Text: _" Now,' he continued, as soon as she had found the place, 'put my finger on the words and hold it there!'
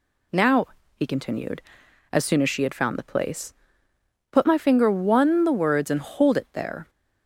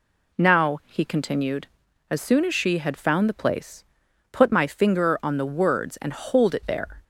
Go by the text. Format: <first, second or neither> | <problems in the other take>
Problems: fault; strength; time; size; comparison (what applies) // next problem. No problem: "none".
second | says "one" for "on"; at 4.9 s